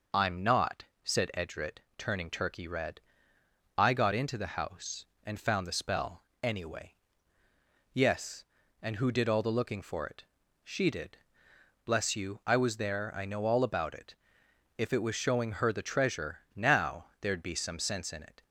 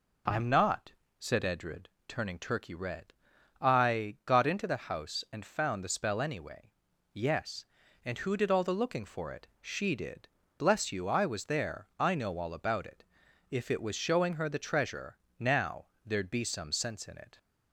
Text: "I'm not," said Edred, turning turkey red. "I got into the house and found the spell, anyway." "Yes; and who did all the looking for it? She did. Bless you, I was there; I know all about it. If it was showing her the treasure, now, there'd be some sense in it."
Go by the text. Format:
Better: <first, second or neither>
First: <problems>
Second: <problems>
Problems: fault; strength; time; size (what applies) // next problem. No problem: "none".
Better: neither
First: none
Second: none